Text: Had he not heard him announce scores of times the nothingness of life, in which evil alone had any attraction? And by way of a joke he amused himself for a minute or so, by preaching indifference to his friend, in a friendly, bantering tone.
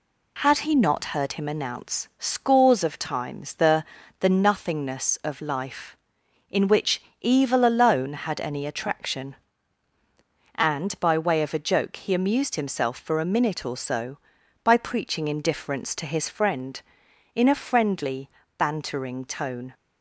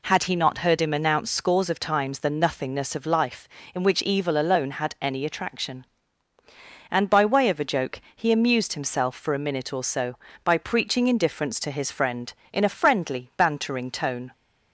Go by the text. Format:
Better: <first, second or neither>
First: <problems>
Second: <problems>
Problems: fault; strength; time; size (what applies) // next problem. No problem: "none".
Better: second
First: says "the" twice; at 4.1 s // pauses between "which" and "evil"; slight; at 7.0 s; 0.20 s long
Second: none